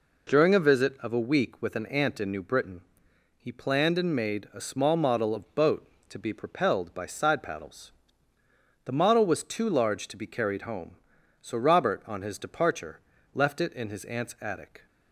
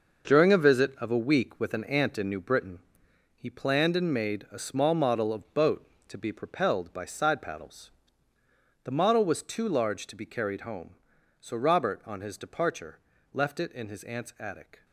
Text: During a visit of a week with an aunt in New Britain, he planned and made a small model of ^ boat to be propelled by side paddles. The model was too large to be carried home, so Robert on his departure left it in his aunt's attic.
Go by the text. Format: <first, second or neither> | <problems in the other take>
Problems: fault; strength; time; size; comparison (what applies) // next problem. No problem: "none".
first | gets quieter; strong; throughout; 9.5 dB // pauses between "departure" and "left"; slight; at 12.9 s; 0.34 s long; slight in the first